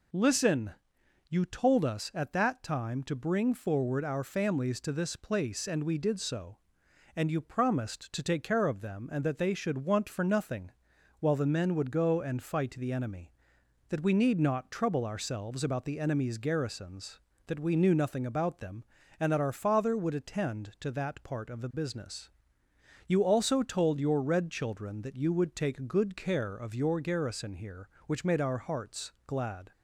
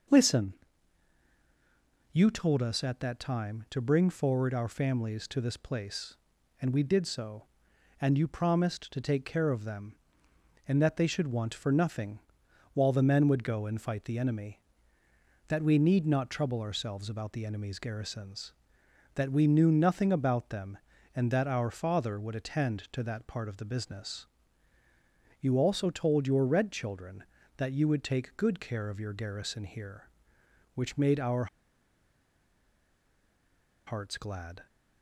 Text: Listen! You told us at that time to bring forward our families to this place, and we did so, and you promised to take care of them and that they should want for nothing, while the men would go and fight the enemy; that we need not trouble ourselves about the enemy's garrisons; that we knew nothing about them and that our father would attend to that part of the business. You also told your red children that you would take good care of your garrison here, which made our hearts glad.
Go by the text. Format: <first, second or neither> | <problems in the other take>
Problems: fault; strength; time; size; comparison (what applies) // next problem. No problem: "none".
first | pauses between "our" and "hearts"; strong; at 31.4 s; 2.4 s long